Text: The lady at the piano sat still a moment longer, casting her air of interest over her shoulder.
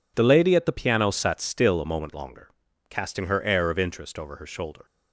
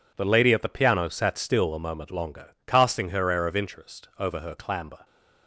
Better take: first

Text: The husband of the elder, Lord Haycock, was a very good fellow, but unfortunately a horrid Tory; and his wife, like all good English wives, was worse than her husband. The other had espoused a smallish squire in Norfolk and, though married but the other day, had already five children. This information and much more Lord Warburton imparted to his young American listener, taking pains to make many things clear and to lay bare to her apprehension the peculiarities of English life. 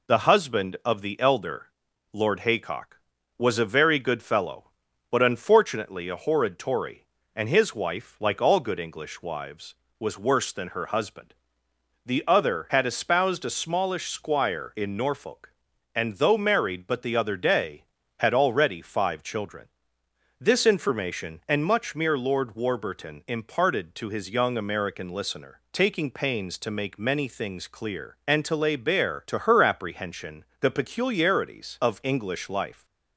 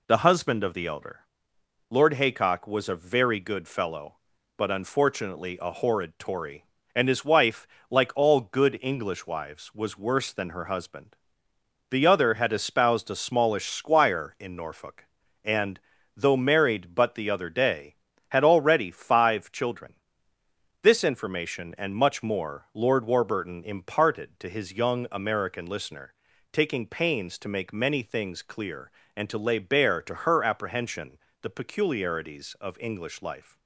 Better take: second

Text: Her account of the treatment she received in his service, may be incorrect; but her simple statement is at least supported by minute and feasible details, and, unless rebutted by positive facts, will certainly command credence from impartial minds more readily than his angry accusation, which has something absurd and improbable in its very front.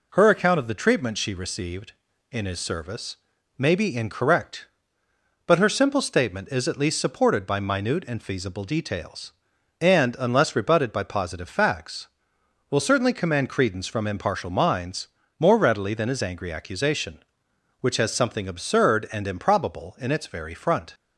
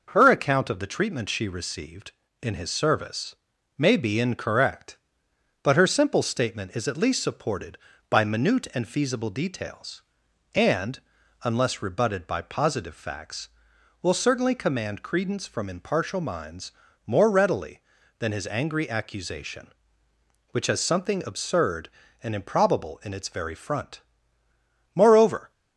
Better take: first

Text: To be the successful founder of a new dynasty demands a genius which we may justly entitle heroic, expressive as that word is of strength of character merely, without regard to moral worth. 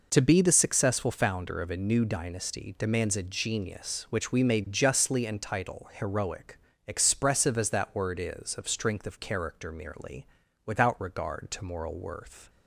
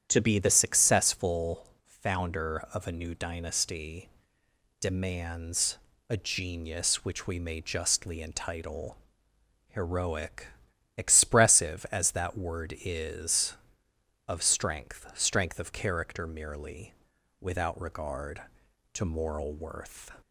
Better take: first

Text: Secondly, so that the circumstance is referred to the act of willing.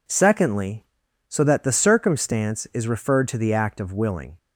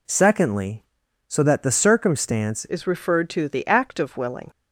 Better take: first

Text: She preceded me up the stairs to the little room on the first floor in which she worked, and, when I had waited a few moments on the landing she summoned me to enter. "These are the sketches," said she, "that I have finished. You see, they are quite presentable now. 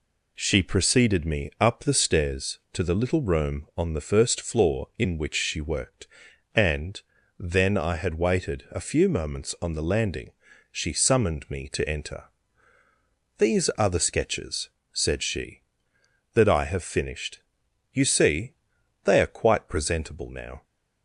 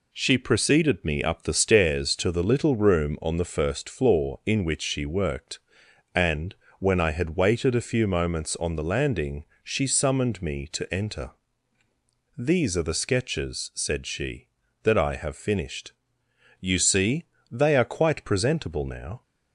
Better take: second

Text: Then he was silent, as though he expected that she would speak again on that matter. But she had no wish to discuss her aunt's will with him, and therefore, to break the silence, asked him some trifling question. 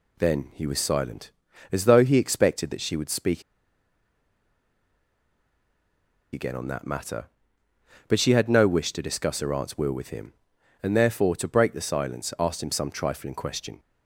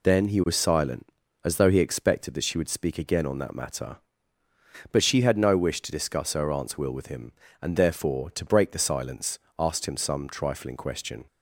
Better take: second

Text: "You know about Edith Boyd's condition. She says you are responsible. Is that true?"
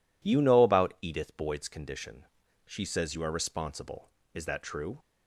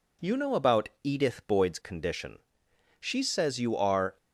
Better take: first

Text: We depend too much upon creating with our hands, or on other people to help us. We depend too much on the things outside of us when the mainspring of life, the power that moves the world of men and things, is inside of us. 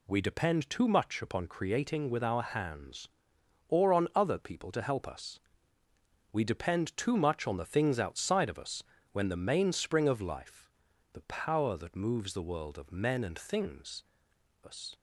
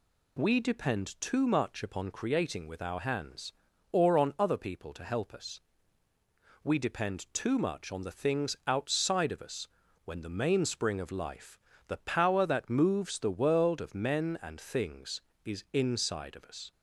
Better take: second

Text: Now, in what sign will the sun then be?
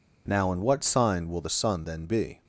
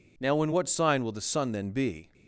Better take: neither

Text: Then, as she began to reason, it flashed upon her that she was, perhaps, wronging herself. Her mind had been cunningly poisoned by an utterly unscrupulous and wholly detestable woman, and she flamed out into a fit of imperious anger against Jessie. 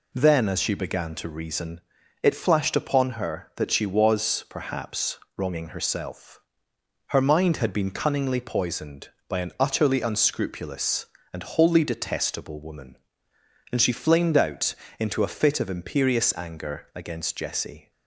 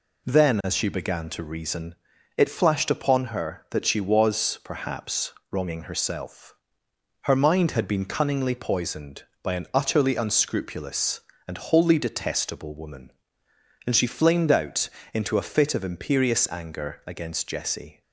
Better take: neither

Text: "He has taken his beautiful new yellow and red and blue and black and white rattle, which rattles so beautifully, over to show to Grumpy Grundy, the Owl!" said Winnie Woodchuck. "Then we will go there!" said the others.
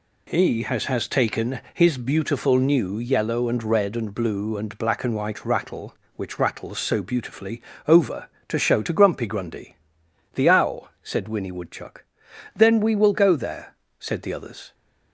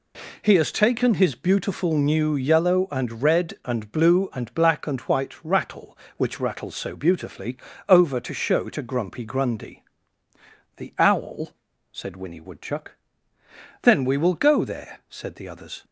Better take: second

